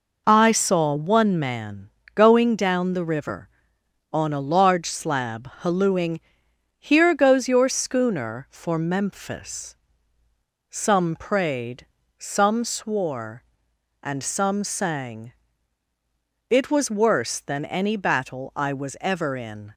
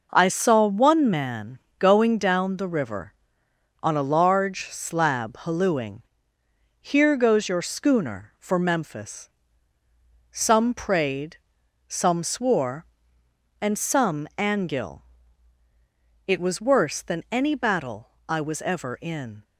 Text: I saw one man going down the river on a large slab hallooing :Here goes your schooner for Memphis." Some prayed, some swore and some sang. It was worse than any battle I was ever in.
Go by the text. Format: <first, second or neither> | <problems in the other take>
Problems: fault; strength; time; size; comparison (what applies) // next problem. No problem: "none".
first | pauses between "man" and "going"; slight; at 1.5 s; 0.22 s long; slight in the first // says "angil" for "sang"; at 14.3 s // pauses between "battle" and "I"; slight; at 18.1 s; 0.18 s long